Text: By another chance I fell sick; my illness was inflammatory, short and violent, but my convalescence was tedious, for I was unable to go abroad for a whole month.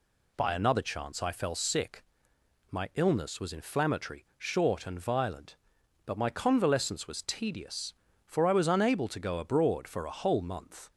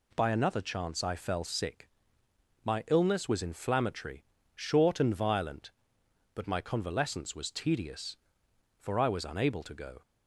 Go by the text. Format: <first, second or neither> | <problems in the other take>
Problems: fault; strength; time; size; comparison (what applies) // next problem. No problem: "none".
first | stops before "abroad for a whole month"; at 10.0 s